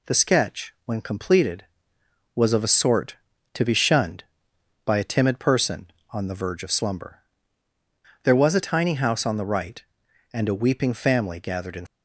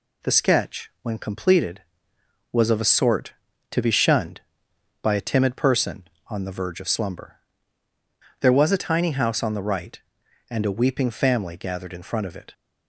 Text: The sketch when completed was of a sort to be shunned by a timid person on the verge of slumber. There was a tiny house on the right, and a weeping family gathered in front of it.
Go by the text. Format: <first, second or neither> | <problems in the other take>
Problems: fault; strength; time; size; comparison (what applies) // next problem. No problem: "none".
second | stops before "front of it"; at 11.8 s